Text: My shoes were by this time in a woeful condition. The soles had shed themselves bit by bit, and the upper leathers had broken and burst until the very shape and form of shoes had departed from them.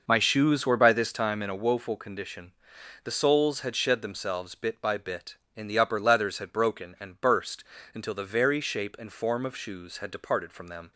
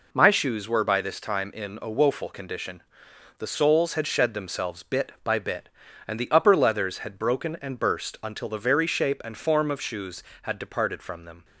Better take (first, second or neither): second